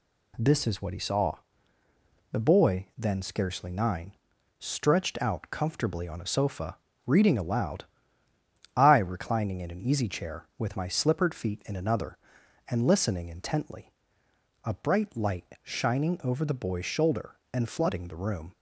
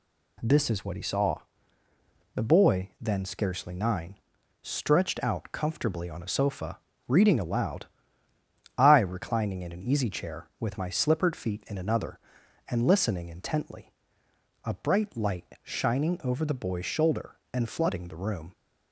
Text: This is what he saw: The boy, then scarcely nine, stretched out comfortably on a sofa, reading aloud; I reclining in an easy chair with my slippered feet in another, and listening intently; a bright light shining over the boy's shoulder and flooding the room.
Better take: neither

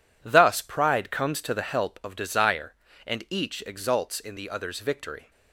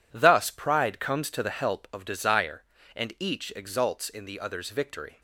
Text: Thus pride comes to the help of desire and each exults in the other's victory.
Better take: neither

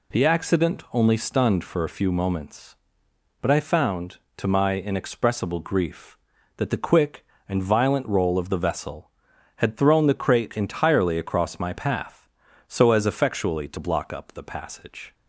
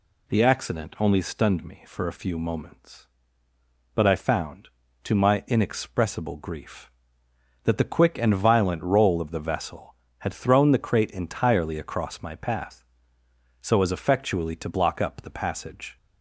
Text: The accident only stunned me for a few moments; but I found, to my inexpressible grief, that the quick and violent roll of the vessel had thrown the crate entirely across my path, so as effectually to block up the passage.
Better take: second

